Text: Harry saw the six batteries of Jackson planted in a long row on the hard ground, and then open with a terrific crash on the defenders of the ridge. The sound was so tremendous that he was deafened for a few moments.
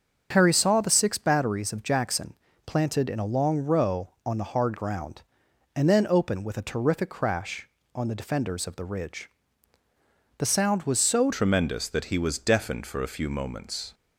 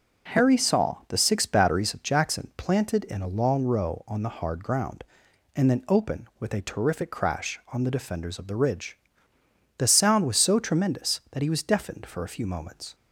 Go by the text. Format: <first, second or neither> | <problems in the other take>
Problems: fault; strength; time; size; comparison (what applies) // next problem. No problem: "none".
second | starts louder than the rest; until 1.3 s; 7 dB // pauses between "Jackson" and "planted"; slight; at 2.3 s; 0.32 s long // changes voice at "tremendous"; from 11.3 s on; 2.6 s long